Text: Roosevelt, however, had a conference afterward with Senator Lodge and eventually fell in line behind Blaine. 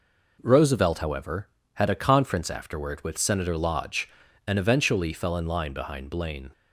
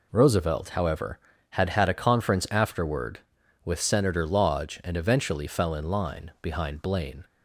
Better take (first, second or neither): first